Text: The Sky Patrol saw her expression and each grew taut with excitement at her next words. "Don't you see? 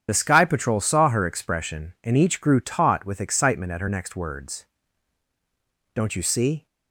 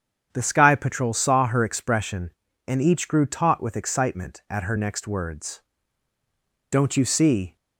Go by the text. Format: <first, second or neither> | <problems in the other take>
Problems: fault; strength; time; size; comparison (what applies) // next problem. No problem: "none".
second | loses the start of "The"; at 0.0 s; 45 ms // starts louder than the rest; strong; until 1.0 s; 8.5 dB; strong in the second